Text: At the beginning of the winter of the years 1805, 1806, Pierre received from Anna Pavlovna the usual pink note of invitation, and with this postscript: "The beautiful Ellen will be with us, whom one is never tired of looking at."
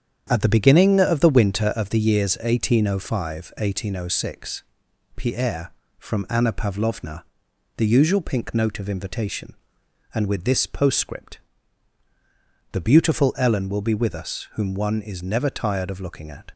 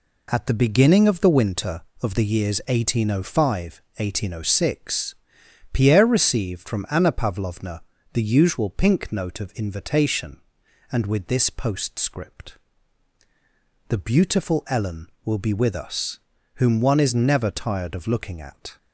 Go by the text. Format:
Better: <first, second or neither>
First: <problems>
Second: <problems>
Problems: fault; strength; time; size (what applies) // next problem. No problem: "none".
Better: second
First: starts louder than the rest; strong; until 1.3 s; 8.5 dB // skips "received"; at 5.8 s // pauses between "Pavlovna" and "the"; noticeable; at 7.2 s; 0.54 s long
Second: pauses between "Pavlovna" and "the"; slight; at 7.8 s; 0.32 s long